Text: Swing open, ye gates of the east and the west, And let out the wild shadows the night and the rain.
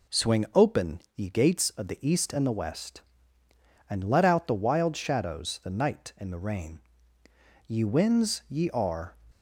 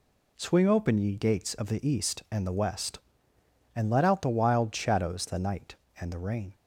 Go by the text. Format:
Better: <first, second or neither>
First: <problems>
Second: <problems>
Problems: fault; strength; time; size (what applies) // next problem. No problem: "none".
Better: second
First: goes on to say "Ye winds ye are"; from 7.6 s on; 1.5 s long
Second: none